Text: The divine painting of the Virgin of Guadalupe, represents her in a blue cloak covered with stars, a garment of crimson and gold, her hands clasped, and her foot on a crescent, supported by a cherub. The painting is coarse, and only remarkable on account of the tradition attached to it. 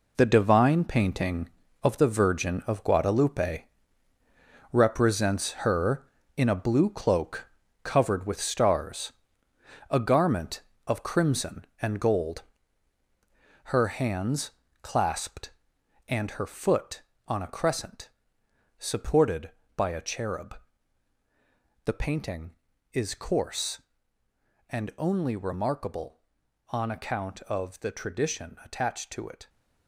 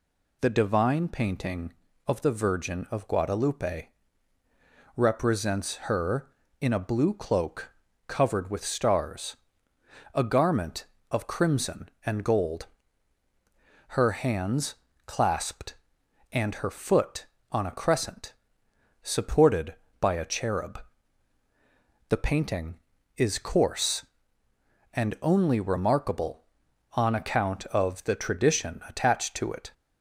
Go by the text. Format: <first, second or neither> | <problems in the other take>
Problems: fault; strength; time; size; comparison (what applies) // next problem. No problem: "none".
second | gets quieter; strong; throughout; 10 dB // pauses between "cloak" and "covered"; slight; at 7.4 s; 0.34 s long; slight in the second // pauses between "hands" and "clasped"; slight; at 14.5 s; 0.32 s long; slight in the second